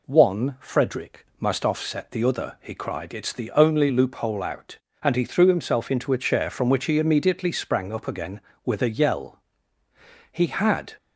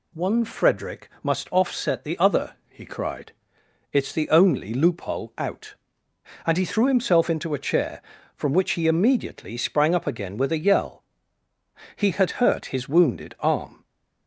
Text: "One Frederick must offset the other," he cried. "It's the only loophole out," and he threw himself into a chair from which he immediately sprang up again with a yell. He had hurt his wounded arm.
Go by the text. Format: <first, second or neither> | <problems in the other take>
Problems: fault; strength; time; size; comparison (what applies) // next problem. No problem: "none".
second | stops before "hurt his wounded arm"; at 10.9 s